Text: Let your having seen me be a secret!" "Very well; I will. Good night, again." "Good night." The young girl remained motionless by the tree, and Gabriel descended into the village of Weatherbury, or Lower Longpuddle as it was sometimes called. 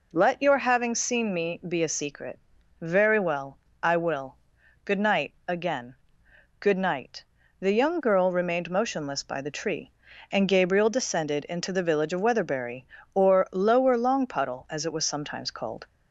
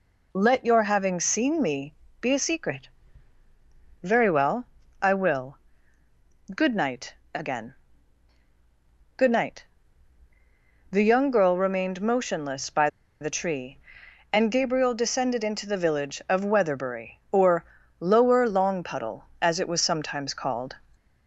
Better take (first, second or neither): first